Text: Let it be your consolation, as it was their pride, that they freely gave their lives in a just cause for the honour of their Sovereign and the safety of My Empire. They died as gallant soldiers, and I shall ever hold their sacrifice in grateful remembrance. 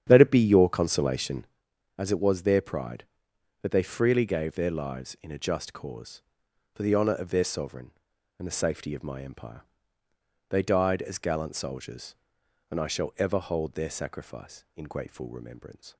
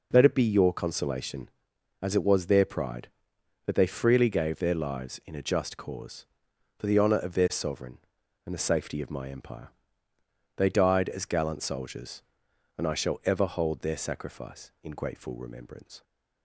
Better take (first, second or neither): second